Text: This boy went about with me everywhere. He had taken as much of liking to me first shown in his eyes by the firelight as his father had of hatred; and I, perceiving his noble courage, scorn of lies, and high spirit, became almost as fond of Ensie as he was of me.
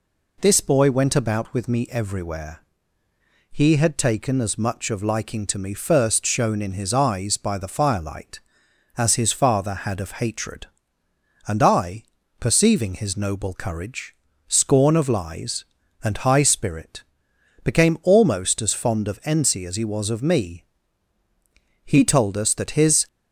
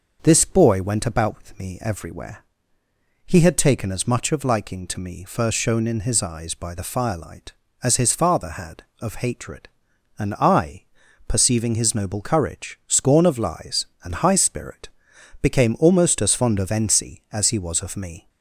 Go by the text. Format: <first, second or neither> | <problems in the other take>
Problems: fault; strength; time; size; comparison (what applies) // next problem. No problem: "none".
second | goes on to say "He told us that his"; noticeable; from 21.8 s on; 1.2 s long